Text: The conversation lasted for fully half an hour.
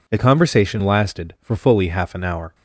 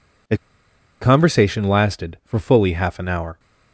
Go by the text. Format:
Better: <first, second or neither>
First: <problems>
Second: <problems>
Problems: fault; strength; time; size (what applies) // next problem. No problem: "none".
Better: first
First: none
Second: pauses between "The" and "conversation"; noticeable; at 0.3 s; 0.63 s long